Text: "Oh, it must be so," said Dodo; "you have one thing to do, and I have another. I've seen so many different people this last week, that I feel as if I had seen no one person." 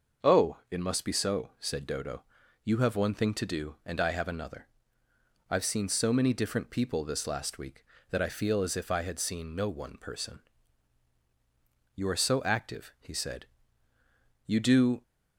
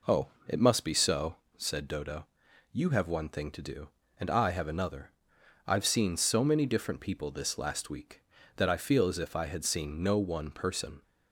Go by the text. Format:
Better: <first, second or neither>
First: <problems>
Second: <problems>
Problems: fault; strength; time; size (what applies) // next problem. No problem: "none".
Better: second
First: starts louder than the rest; until 1.3 s; 6 dB // goes on to say "You are so active he said you do"; strong; from 11.9 s on; 3.0 s long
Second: none